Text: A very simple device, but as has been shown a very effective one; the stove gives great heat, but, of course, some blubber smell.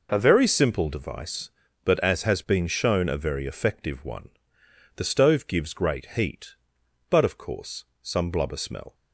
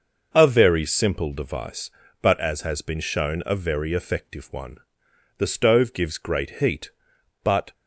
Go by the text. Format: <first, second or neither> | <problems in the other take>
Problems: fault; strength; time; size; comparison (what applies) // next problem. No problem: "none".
first | stops before "of course some blubber smell"; at 7.7 s